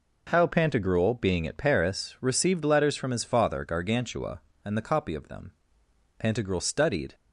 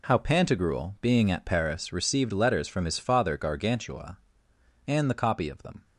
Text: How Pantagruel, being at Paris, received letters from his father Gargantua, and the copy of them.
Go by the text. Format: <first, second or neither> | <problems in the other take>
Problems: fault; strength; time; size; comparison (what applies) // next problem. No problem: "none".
second | goes on to say "Pantagruel studied"; noticeable; from 6.1 s on; 0.96 s long